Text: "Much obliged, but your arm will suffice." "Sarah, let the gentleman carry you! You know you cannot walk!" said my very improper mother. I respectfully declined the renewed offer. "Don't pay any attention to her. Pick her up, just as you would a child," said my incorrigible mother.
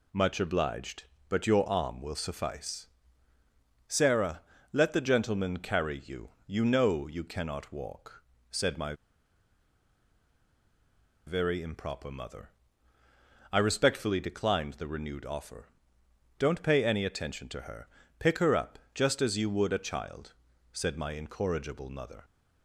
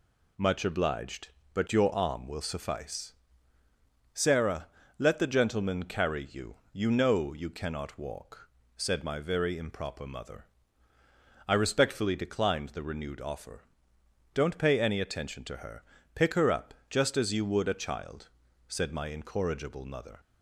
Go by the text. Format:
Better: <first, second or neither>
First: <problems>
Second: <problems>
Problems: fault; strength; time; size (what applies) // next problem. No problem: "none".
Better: second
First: pauses between "my" and "very"; strong; at 8.9 s; 2.3 s long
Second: none